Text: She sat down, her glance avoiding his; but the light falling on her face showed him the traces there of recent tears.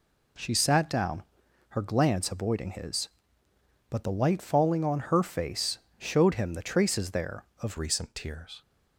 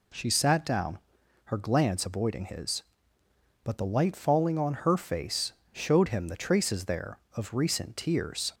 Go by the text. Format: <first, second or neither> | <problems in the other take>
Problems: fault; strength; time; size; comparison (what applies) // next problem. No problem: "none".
second | pauses between "face" and "showed"; slight; at 5.7 s; 0.18 s long; slight in the second // changes voice at "recent"; from 7.7 s on; 0.9 s long